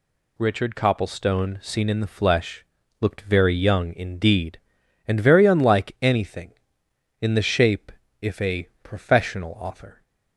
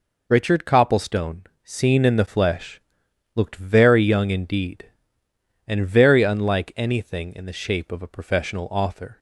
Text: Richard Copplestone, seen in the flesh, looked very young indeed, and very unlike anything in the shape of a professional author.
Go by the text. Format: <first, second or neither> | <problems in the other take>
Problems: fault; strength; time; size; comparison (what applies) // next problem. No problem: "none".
second | says "if" for "of"; at 8.2 s